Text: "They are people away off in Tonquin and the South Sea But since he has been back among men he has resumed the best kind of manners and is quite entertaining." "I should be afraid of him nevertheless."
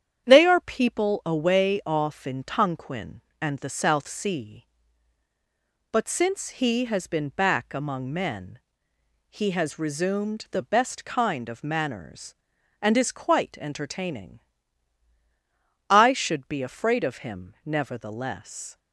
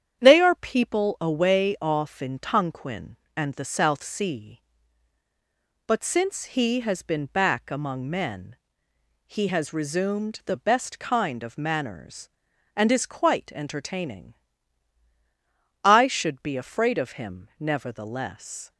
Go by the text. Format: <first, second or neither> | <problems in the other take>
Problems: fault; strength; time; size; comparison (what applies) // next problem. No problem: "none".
neither | starts louder than the rest; strong; the same in both // pauses between "men" and "he"; noticeable; the same in both